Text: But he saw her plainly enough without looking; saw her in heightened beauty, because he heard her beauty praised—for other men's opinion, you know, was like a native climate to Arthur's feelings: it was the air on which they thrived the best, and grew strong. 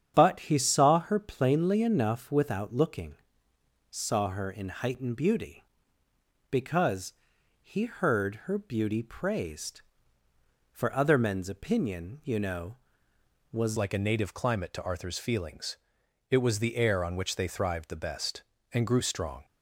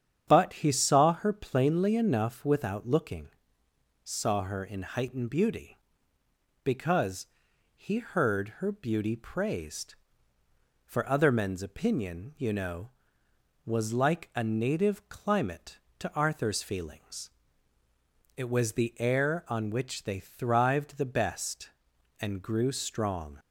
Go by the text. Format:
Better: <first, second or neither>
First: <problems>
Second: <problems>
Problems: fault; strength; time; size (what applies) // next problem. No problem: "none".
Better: second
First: starts louder than the rest; strong; until 1.1 s; 8.5 dB // pauses between "because" and "he"; noticeable; at 7.1 s; 0.50 s long // changes voice at "like"; from 13.7 s on; 5.7 s long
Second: starts louder than the rest; strong; until 1.2 s; 8.5 dB // pauses between "because" and "he"; noticeable; at 7.2 s; 0.50 s long